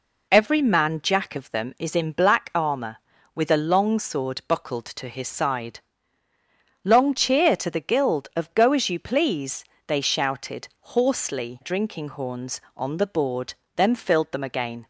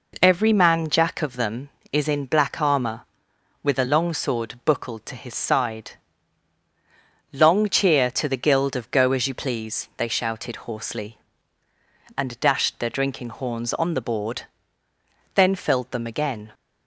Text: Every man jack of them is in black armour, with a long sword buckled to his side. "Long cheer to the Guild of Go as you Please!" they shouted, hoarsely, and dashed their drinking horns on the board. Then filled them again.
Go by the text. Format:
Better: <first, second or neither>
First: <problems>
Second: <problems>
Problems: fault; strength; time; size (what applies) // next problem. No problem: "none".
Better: second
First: skips "and dashed their"; at 11.6 s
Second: none